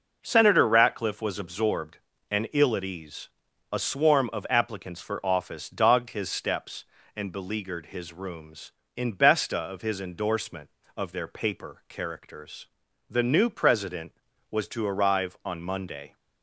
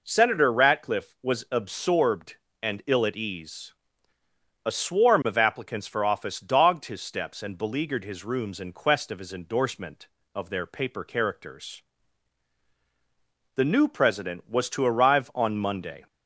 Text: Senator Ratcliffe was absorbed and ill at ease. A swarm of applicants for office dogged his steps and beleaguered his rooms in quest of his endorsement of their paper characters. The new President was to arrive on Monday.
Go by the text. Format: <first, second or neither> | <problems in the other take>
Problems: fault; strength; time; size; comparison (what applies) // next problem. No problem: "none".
second | says "besta" for "quest"; at 9.1 s